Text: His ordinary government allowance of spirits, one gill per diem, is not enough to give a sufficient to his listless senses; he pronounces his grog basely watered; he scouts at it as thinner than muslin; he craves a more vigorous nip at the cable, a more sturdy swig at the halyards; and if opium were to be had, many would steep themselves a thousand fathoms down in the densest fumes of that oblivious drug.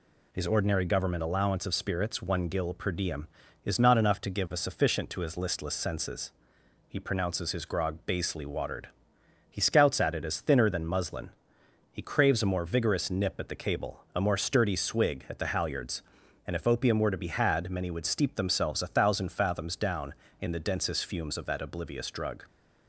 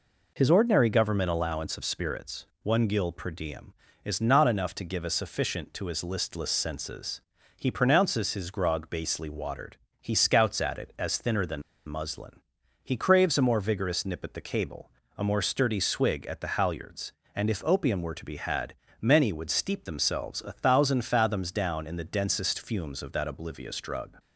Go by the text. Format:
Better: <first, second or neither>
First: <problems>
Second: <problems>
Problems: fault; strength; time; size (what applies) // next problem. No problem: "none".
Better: first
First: none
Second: pauses between "than" and "muslin"; slight; at 11.6 s; 0.24 s long